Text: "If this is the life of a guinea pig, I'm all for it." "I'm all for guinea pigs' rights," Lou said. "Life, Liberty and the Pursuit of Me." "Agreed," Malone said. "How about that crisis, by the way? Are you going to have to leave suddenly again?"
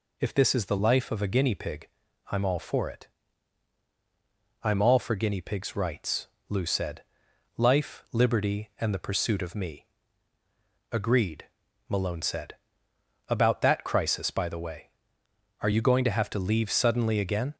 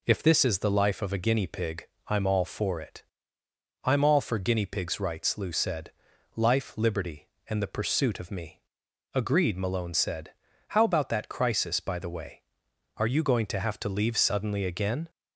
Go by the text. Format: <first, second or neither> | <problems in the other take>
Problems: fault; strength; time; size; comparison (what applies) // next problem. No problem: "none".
second | skips "How"; at 12.9 s